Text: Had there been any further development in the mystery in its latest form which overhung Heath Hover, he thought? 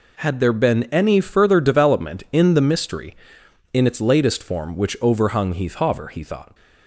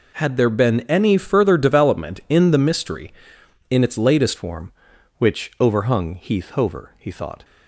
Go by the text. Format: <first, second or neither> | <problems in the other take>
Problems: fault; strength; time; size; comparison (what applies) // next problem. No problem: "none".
first | changes voice at "form"; from 4.3 s on; 3.1 s long